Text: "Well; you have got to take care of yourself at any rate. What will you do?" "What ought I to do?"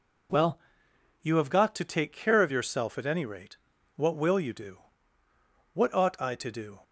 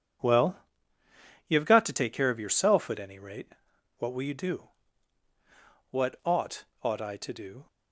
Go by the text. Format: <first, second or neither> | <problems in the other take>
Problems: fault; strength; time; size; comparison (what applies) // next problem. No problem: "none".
first | says "ought" twice; at 6.8 s